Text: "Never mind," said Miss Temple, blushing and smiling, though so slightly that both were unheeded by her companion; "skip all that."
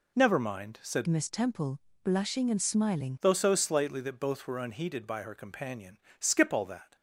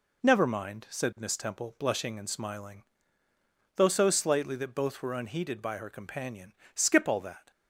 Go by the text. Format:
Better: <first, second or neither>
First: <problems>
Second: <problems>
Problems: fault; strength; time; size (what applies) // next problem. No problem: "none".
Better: second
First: changes voice from "Miss" to "smiling"; from 1.0 to 3.1 s; 2.1 s long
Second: none